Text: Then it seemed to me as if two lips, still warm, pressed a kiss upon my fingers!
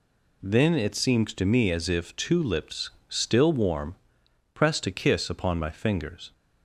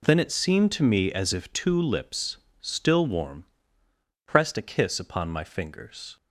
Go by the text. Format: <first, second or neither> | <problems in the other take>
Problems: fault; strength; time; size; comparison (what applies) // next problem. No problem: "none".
neither | none